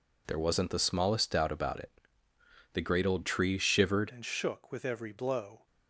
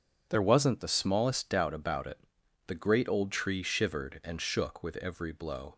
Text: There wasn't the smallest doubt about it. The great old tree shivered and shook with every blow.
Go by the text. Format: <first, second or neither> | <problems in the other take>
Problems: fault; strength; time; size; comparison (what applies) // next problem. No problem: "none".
second | changes voice at "and"; from 4.1 s on; 1.5 s long